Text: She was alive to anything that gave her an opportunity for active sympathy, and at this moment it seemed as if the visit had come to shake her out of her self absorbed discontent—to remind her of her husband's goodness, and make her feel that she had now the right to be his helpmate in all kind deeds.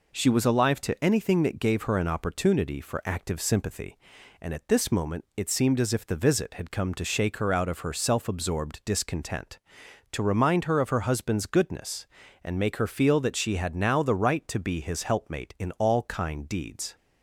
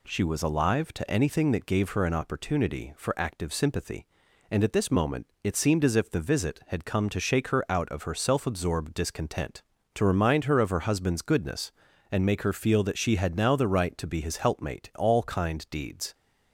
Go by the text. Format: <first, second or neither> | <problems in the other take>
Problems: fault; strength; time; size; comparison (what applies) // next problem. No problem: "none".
first | pauses between "moment" and "it"; slight; at 5.2 s; 0.16 s long // skips "in"; at 14.9 s